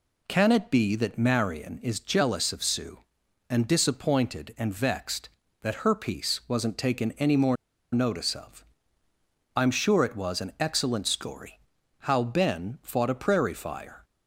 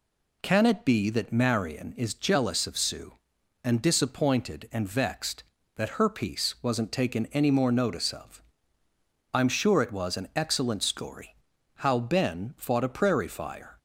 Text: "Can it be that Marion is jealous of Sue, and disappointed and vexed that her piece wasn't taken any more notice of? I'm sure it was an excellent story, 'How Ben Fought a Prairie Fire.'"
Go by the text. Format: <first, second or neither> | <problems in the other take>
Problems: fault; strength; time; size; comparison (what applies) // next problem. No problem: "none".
second | pauses between "more" and "notice"; at 7.5 s; 0.38 s long